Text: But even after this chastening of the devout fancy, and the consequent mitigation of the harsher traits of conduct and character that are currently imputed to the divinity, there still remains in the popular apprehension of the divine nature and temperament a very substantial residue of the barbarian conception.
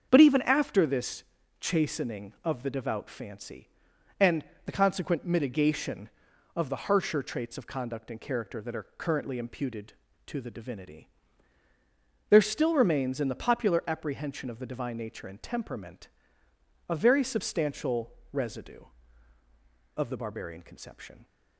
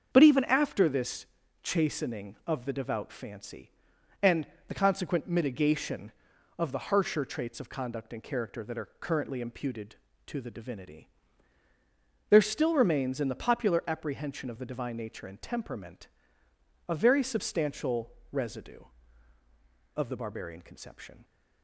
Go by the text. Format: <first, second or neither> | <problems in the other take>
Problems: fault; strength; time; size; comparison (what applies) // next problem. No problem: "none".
neither | starts louder than the rest; the same in both // pauses between "this" and "chastening"; slight; the same in both // pauses between "and" and "the"; slight; the same in both // pauses between "temperament" and "a"; noticeable; the same in both // pauses between "substantial" and "residue"; slight; the same in both